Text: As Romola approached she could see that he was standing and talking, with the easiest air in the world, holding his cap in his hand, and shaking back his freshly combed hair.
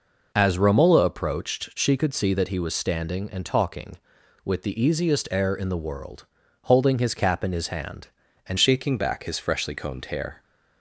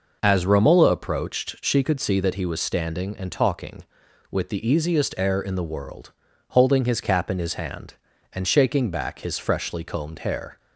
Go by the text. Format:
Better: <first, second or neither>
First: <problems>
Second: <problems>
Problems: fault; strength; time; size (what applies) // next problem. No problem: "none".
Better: second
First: changes voice at "shaking"; from 8.5 s on; 1.9 s long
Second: none